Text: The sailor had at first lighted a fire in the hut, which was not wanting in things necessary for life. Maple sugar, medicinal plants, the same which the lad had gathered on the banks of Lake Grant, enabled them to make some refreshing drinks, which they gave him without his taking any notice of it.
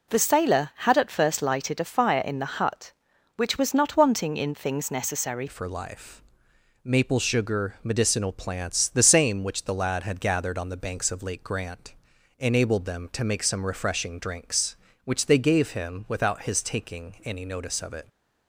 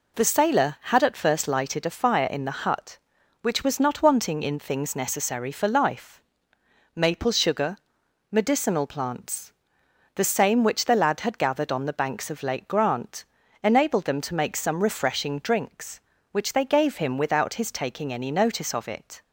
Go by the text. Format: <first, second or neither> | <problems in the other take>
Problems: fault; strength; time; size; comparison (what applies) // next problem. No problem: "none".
second | changes voice at "for"; from 5.4 s on; 12.6 s long